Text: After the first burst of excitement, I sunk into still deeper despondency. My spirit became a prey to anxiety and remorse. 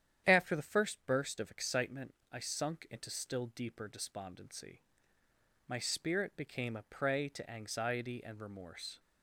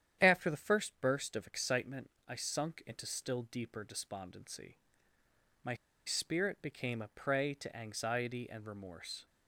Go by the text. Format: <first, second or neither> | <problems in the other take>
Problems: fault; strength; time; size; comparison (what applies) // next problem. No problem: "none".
first | starts louder than the rest; strong; until 1.2 s; 9.5 dB; strong in the first // pauses between "My" and "spirit"; slight; at 5.7 s; 0.29 s long